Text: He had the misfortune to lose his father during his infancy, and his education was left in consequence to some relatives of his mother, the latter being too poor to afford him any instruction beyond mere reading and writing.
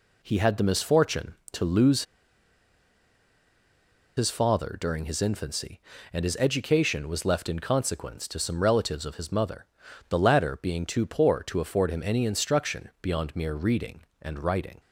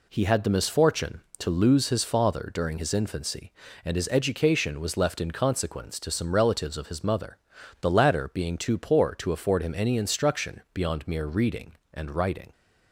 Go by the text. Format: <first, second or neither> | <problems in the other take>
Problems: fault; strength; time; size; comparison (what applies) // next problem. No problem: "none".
second | pauses between "lose" and "his"; strong; at 2.0 s; 2.1 s long